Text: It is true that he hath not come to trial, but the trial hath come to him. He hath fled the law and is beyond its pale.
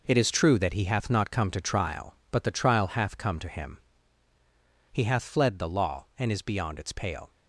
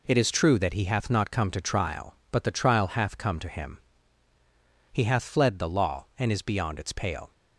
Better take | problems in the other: second | gets quieter; strong; throughout; 8.5 dB

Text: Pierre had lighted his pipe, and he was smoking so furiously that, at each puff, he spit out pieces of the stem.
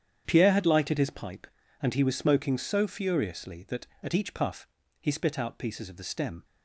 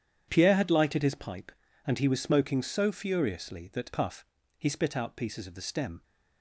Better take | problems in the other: first | starts louder than the rest; strong; until 1.3 s; 9 dB; strong in the first // skips "at each"; at 3.9 s

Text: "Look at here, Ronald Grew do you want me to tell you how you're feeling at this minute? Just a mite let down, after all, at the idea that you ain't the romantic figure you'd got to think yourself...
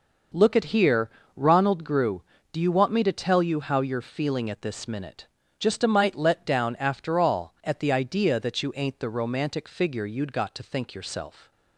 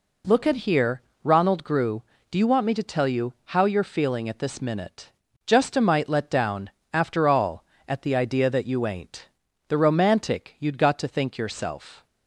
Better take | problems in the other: first | pauses between "ain't" and "the"; at 9.2 s; 0.40 s long // skips "figure"; at 10.5 s

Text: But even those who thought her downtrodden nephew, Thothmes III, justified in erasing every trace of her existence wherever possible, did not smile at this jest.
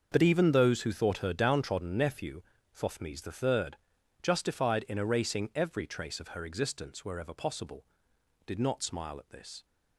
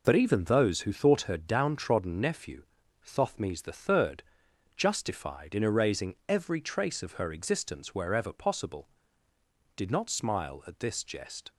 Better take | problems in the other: second | starts louder than the rest; until 1.1 s; 6.5 dB // stops before "jest"; at 9.6 s

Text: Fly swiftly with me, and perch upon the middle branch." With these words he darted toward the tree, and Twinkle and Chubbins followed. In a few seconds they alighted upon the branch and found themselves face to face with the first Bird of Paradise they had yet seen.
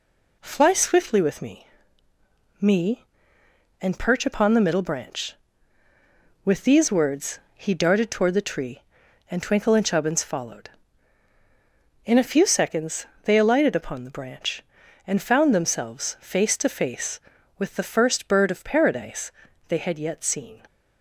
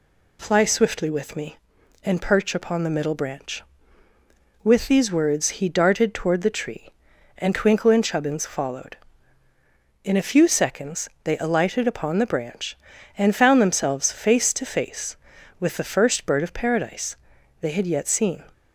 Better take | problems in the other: second | says "me" twice; at 2.6 s // pauses between "words" and "he"; slight; at 7.3 s; 0.16 s long // pauses between "seconds" and "they"; slight; at 13.0 s; 0.16 s long // pauses between "Paradise" and "they"; at 19.3 s; 0.38 s long; also in the second

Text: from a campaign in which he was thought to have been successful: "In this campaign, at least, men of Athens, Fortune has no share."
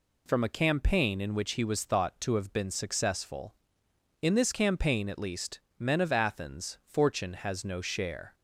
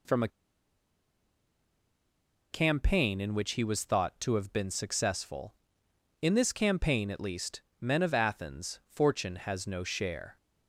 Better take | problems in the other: first | pauses between "a" and "campaign"; strong; at 0.2 s; 2.2 s long

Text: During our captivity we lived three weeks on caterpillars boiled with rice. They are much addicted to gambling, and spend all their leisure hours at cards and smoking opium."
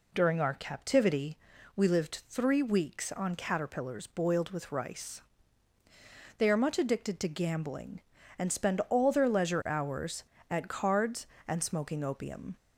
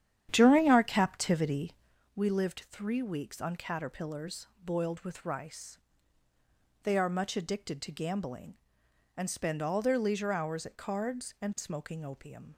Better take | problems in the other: first | starts louder than the rest; strong; until 2.0 s; 10 dB // pauses between "captivity" and "we"; at 1.7 s; 0.42 s long; also in the first // pauses between "caterpillars" and "boiled"; slight; at 4.4 s; 0.18 s long

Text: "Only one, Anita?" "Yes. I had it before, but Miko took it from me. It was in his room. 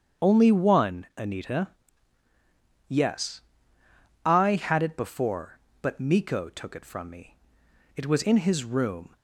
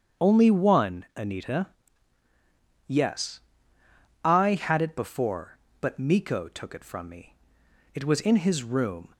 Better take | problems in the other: neither | starts louder than the rest; strong; the same in both

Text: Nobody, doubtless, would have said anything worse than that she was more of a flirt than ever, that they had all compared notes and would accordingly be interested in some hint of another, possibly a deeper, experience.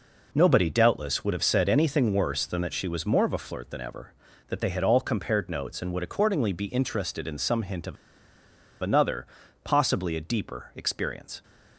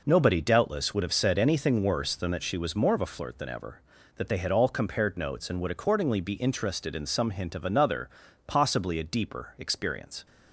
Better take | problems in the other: second | pauses between "of" and "another"; noticeable; at 7.9 s; 0.86 s long

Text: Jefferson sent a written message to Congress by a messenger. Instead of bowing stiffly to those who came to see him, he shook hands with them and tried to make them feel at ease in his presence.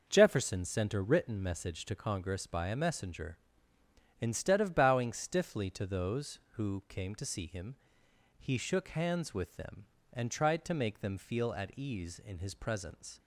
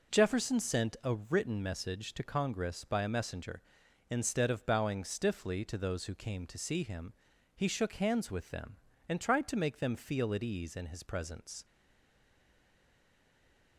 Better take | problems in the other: first | stays silent after the last word; from 11.6 s on; 2.1 s long

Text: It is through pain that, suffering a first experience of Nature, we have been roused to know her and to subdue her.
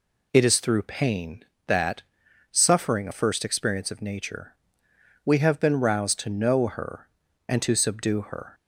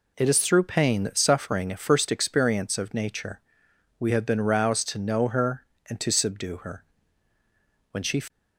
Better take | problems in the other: first | goes on to say "When she"; slight; from 7.9 s on; 0.30 s long

